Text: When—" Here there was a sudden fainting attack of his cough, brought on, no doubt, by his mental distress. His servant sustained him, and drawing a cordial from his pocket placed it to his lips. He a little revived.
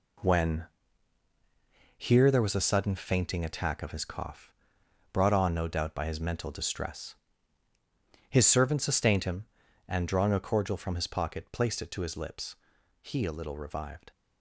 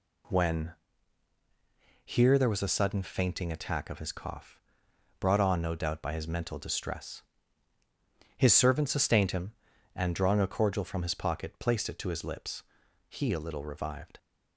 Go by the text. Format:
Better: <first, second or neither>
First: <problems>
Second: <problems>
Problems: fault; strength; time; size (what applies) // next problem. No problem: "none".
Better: second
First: gets quieter; strong; throughout; 8 dB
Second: none